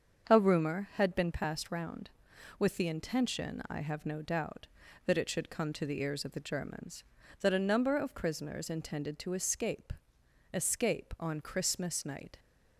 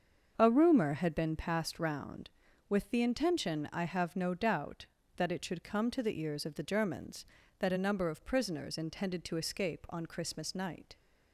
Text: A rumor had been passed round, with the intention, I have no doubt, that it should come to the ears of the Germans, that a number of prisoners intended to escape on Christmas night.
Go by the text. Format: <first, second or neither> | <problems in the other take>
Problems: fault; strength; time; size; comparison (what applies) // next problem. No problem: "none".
second | starts louder than the rest; until 1.3 s; 7 dB; also in the second // says "escape" twice; at 10.5 s